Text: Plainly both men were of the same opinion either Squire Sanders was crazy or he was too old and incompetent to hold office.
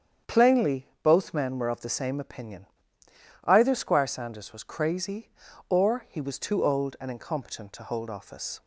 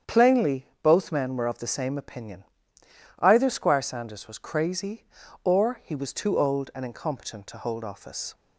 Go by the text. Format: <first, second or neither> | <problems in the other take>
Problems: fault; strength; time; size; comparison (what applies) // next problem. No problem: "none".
neither | starts louder than the rest; strong; the same in both // pauses between "opinion" and "either"; noticeable; the same in both